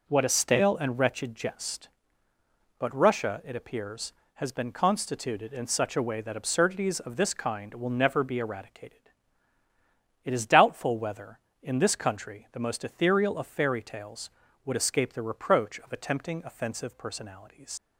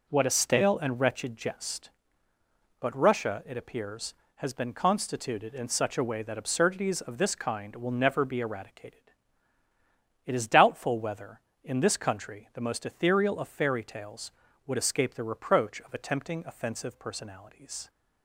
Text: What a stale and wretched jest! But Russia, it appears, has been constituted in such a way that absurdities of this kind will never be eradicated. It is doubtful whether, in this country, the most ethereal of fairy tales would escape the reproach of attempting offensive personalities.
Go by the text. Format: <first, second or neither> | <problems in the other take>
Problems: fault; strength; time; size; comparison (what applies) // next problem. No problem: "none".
second | leaves "personalities" unfinished; at 17.7 s; 100 ms